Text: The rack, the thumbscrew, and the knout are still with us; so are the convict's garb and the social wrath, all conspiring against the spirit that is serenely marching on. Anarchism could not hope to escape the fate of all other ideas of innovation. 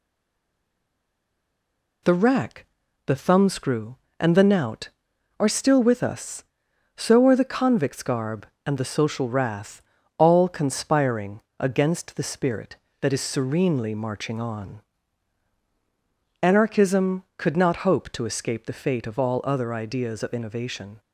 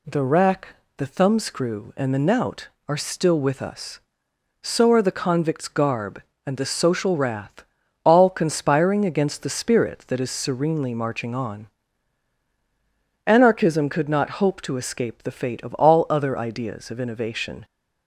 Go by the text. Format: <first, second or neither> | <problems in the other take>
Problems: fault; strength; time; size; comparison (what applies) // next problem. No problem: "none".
second | stays silent before the first word; noticeable; until 2.0 s; 2.0 s long // pauses between "conspiring" and "against"; slight; at 11.3 s; 0.18 s long